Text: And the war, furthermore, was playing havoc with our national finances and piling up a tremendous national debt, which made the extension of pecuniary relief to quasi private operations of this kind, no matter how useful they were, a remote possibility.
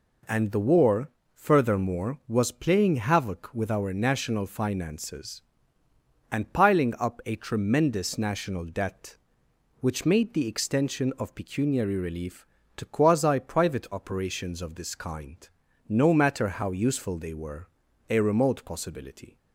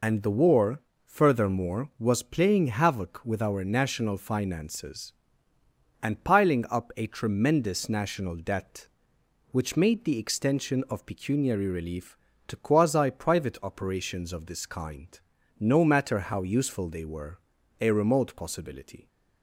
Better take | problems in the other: first | loses the start of "And"; at 0.0 s; 85 ms

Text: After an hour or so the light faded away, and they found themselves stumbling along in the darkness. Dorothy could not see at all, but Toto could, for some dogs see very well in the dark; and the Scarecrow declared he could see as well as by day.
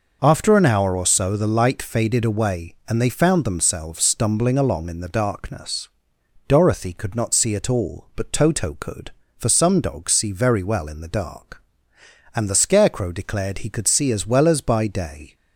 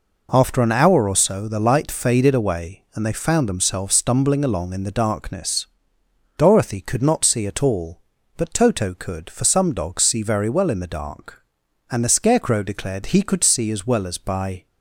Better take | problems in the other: first | stops before "day"; at 14.6 s

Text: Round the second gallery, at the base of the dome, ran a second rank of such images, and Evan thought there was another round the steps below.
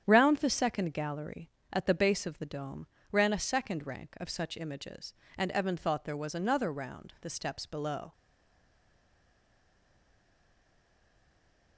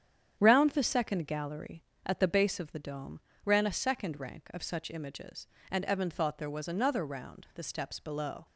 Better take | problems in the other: second | starts louder than the rest; strong; until 1.0 s; 9 dB; strong in the second // stays silent after the last word; strong; from 8.1 s on; 3.6 s long

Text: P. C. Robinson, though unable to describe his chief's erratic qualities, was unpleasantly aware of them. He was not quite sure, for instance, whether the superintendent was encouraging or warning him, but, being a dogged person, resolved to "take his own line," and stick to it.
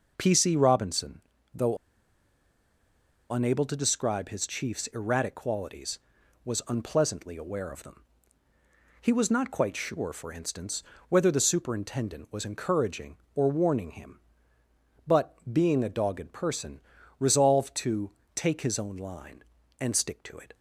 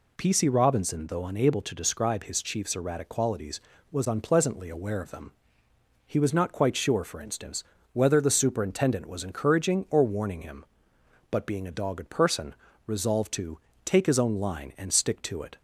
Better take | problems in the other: second | pauses between "though" and "unable"; strong; at 1.7 s; 1.5 s long // pauses between "to" and "take"; slight; at 18.1 s; 0.24 s long; slight in the second

